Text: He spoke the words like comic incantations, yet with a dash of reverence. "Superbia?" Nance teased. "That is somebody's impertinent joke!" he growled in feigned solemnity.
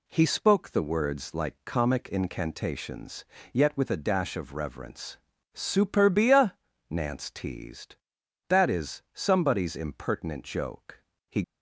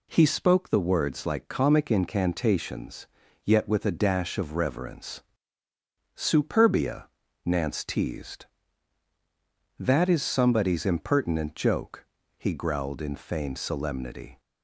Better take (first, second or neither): second